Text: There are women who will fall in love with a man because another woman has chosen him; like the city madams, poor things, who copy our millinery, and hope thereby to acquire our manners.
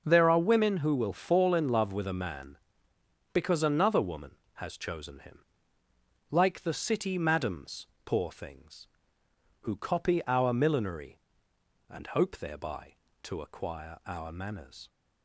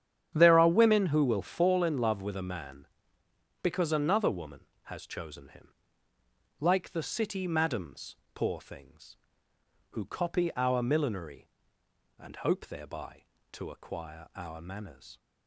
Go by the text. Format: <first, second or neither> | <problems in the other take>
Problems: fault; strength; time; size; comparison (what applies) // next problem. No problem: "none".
first | starts louder than the rest; strong; until 1.7 s; 9 dB